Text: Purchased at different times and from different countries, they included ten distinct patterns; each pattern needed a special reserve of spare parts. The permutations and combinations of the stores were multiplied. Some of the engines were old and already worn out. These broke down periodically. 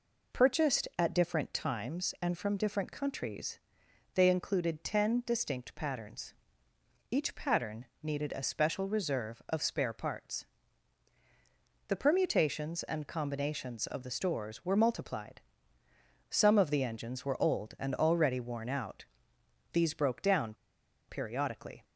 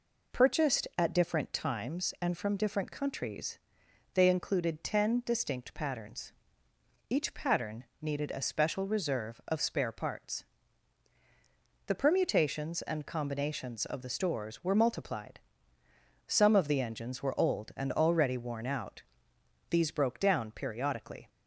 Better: second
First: pauses between "pattern" and "needed"; slight; at 7.8 s; 0.18 s long // pauses between "down" and "periodically"; noticeable; at 20.5 s; 0.55 s long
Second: pauses between "pattern" and "needed"; slight; at 7.8 s; 0.18 s long

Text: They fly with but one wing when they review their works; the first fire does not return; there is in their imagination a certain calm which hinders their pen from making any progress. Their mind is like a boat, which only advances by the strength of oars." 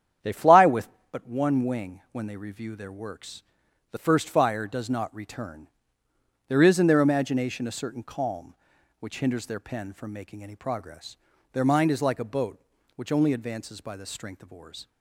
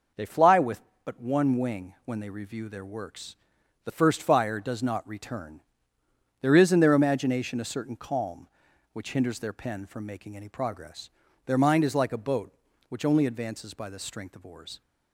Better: second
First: starts louder than the rest; strong; until 1.2 s; 9 dB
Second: none

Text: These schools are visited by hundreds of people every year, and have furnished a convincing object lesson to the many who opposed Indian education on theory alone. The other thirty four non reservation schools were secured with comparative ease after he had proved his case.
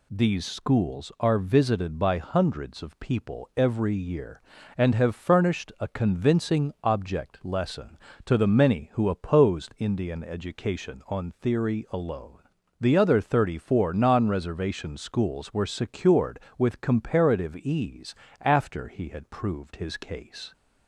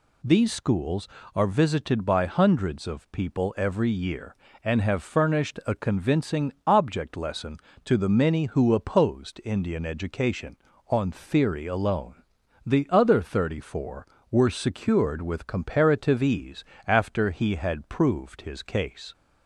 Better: first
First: pauses between "ease" and "after"; slight; at 18.1 s; 0.28 s long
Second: skips "non reservation schools"; at 14.1 s // pauses between "ease" and "after"; slight; at 16.6 s; 0.24 s long

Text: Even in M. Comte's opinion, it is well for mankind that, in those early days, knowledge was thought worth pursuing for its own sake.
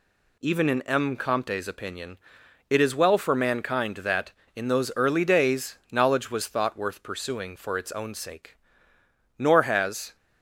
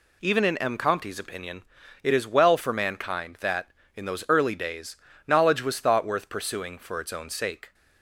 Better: second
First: goes on to say "Nor has"; noticeable; from 9.3 s on; 0.78 s long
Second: none

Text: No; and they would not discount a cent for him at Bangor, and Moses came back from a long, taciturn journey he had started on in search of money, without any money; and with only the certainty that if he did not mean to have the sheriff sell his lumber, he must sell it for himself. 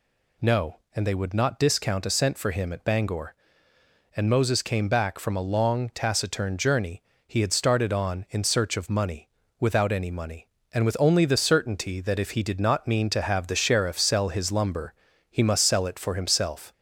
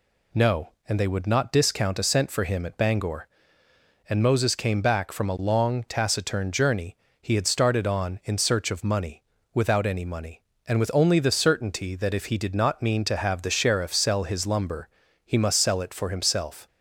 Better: second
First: gets louder; slight; throughout; 2 dB // pauses between "journey" and "he"; slight; at 7.0 s; 0.24 s long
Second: pauses between "journey" and "he"; slight; at 6.9 s; 0.24 s long

